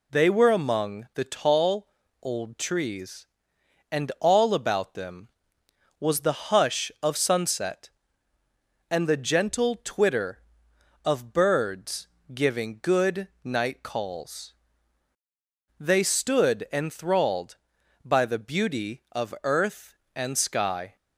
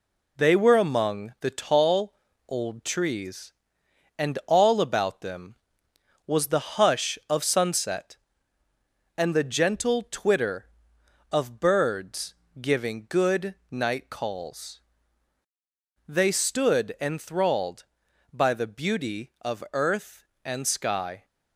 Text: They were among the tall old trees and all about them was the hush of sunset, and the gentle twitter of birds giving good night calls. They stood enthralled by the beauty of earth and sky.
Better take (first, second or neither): first